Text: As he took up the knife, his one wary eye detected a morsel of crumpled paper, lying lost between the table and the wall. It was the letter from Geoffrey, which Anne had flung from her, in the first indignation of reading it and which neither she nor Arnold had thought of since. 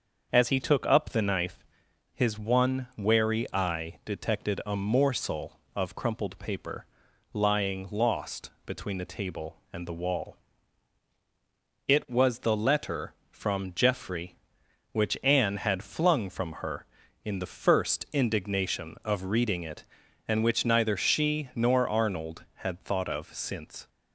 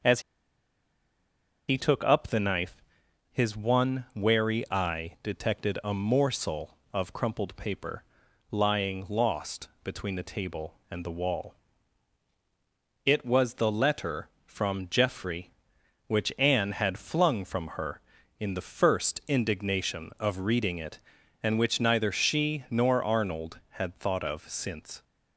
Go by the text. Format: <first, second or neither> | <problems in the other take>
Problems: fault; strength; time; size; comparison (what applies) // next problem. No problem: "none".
first | starts louder than the rest; until 2.5 s; 6.5 dB; also in the first // pauses between "As" and "he"; strong; at 0.2 s; 1.4 s long // pauses between "lost" and "between"; slight; at 9.6 s; 0.16 s long; slight in the first